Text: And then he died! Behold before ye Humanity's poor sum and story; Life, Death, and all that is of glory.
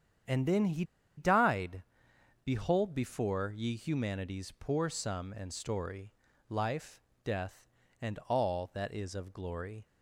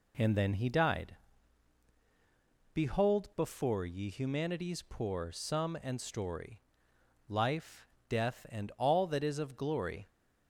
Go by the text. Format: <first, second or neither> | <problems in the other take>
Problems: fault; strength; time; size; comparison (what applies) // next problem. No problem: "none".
second | starts louder than the rest; strong; until 1.6 s; 8.5 dB // pauses between "he" and "died"; slight; at 0.8 s; 0.33 s long